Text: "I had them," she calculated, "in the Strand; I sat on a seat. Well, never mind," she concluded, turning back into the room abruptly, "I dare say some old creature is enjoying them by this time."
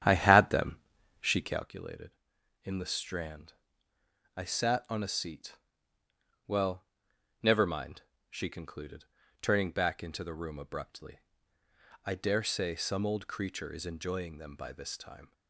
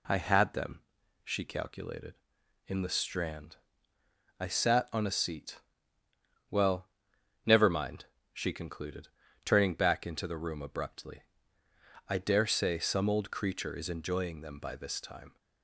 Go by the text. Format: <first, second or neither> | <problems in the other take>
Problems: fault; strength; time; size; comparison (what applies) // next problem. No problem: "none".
second | starts louder than the rest; strong; until 1.7 s; 10 dB